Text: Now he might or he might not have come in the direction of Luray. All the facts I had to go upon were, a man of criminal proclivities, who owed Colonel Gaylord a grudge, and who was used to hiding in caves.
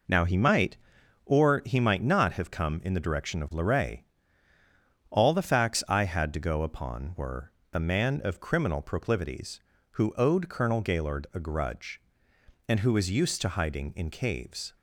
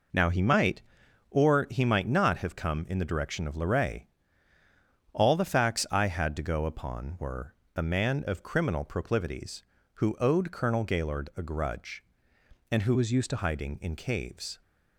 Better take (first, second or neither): first